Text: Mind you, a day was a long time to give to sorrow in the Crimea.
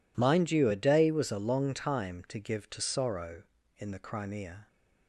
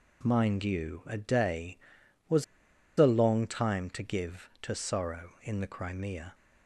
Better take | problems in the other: first | pauses between "was" and "a"; noticeable; at 2.4 s; 0.53 s long

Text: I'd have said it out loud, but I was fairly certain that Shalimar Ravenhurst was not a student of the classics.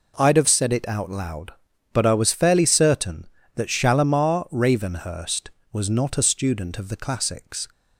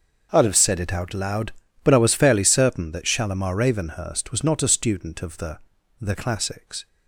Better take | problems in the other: first | starts louder than the rest; until 1.3 s; 6.5 dB // says "the" twice; at 5.9 s

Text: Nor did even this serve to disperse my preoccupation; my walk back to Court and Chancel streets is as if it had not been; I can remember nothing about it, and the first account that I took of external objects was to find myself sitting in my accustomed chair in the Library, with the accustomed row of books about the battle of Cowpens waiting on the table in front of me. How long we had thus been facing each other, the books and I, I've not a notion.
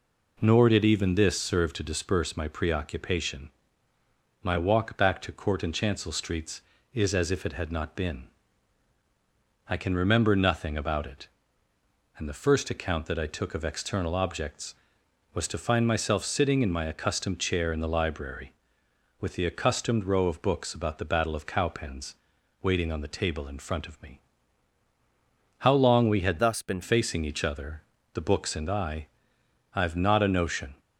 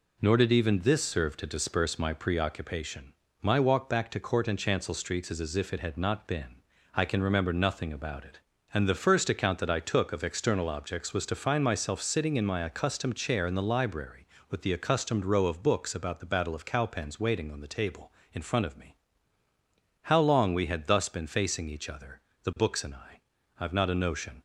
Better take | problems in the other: second | pauses between "Cowpens" and "waiting"; noticeable; at 22.1 s; 0.48 s long // changes voice from "thus" to "been"; from 26.3 to 26.7 s; 0.4 s long

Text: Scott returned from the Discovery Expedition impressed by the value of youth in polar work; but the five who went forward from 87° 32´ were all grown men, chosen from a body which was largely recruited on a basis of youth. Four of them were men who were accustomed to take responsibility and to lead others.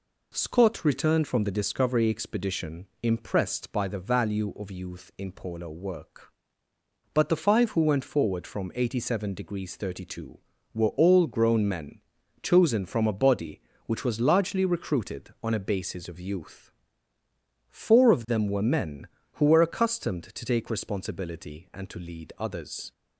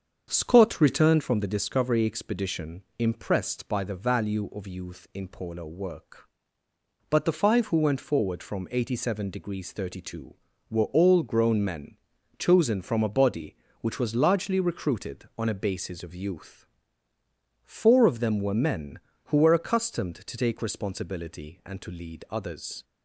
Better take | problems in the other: first | starts louder than the rest; until 1.3 s; 7 dB // pauses between "Expedition" and "impressed"; slight; at 2.8 s; 0.16 s long; slight in the first

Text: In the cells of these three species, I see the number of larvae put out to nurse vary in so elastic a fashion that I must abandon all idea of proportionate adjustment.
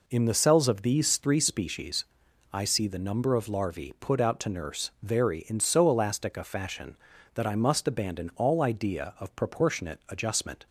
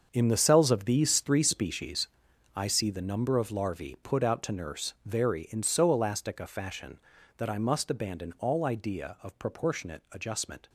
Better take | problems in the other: first | gets quieter; strong; throughout; 12.5 dB

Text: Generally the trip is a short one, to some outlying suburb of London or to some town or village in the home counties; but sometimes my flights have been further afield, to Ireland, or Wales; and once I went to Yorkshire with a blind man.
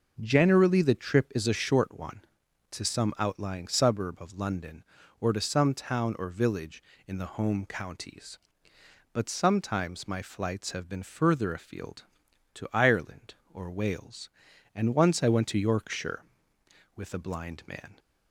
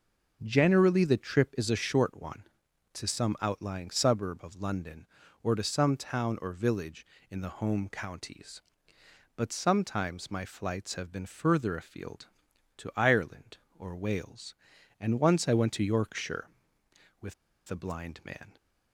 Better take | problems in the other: first | pauses between "with" and "a"; at 17.3 s; 0.38 s long

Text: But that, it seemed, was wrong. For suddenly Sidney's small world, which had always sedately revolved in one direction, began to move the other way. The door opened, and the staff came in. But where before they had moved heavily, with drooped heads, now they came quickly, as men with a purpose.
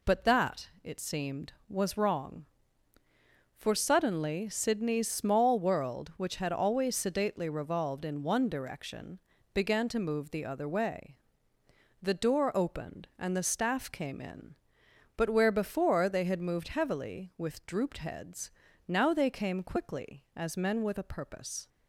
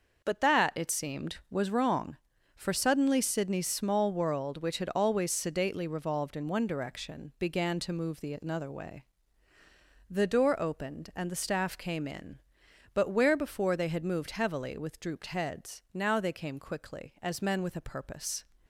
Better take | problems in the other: first | starts louder than the rest; noticeable; until 1.2 s; 6 dB // says "another" for "other"; at 8.4 s

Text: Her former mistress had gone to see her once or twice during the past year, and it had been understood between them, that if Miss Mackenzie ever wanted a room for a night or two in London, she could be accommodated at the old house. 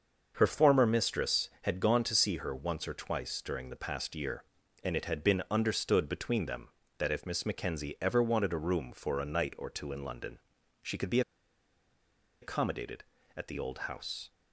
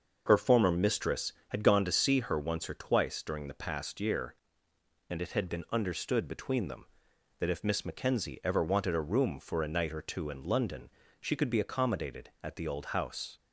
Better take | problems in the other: second | starts louder than the rest; until 1.3 s; 6.5 dB; also in the second // pauses between "be" and "accommodated"; at 11.2 s; 1.2 s long

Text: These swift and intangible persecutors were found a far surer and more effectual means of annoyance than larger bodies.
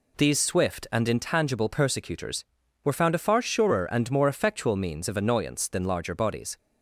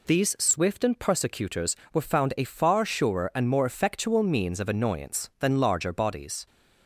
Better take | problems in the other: first | skips "intangible"; at 0.9 s

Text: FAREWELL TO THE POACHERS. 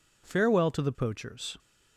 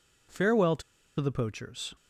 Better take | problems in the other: first | pauses between "TO" and "THE"; at 0.8 s; 0.37 s long

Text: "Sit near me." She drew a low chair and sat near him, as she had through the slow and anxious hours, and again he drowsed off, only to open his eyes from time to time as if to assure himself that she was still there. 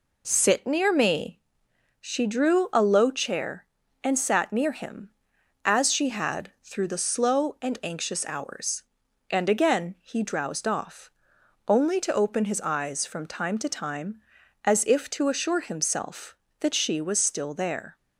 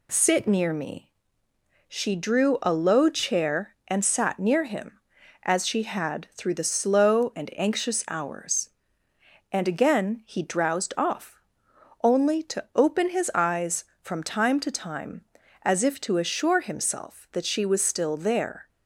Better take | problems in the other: neither | none

